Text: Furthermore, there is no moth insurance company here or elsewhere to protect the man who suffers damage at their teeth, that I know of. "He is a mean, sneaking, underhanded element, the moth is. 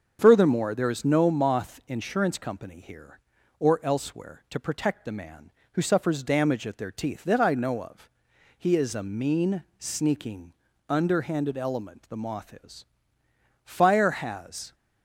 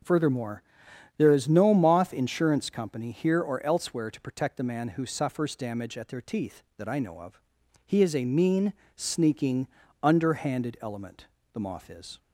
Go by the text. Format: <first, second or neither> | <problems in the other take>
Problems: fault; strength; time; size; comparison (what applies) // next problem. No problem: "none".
second | starts louder than the rest; until 1.2 s; 6.5 dB // goes on to say "Fire has"; noticeable; from 13.6 s on; 1.1 s long